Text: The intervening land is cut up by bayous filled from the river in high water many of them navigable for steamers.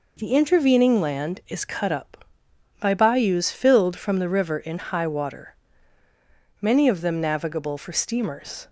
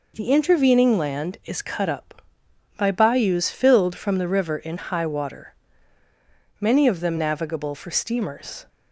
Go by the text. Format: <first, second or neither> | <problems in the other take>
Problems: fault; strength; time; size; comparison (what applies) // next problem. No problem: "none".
neither | pauses between "water" and "many"; the same in both